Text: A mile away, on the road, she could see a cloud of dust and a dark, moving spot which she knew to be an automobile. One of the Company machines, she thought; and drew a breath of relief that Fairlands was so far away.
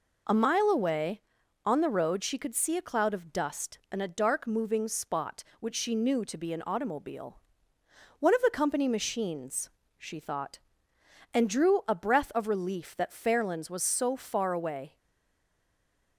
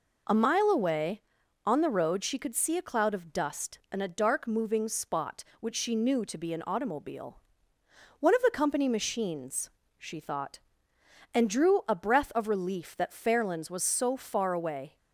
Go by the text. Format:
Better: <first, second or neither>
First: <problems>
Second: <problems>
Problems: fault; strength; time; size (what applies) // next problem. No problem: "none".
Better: second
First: stays silent after the last word; noticeable; from 14.9 s on; 1.2 s long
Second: none